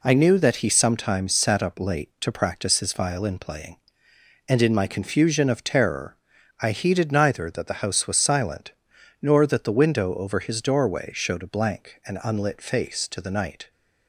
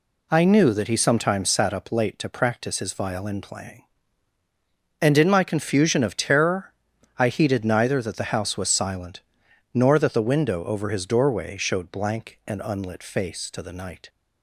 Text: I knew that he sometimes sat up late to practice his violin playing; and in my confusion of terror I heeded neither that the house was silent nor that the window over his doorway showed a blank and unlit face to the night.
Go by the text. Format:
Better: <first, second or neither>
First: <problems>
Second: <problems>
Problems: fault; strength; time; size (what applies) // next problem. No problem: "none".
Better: first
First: pauses between "terror" and "I"; at 6.1 s; 0.44 s long // pauses between "silent" and "nor"; noticeable; at 8.7 s; 0.50 s long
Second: pauses between "terror" and "I"; noticeable; at 6.7 s; 0.46 s long // pauses between "silent" and "nor"; noticeable; at 9.2 s; 0.54 s long // skips "a"; at 11.9 s